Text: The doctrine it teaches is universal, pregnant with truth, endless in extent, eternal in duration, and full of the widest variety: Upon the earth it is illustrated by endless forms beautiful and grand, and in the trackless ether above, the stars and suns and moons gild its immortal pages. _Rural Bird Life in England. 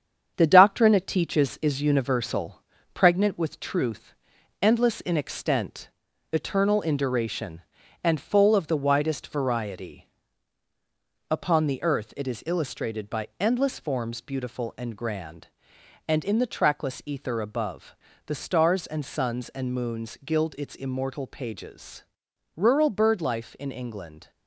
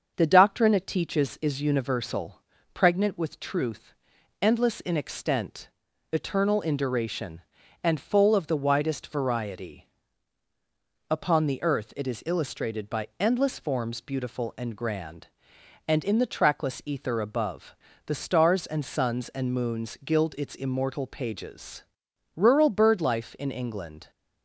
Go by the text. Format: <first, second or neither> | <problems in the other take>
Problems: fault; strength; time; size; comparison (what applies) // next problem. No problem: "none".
second | gets quieter; noticeable; throughout; 4.5 dB // starts louder than the rest; strong; until 1.3 s; 8 dB; also in the second